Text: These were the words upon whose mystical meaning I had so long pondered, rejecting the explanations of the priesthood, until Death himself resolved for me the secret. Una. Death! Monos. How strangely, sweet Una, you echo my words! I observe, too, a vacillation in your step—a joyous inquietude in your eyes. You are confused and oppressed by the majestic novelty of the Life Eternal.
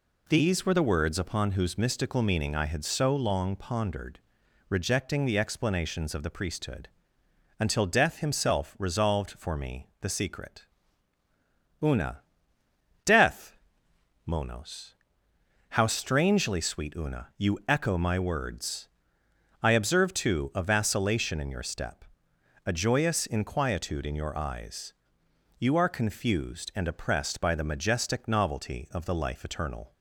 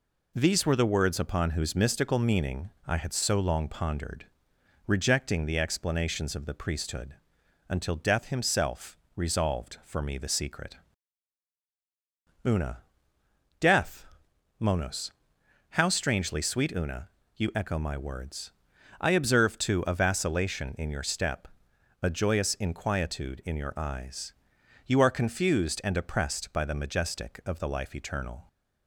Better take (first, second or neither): first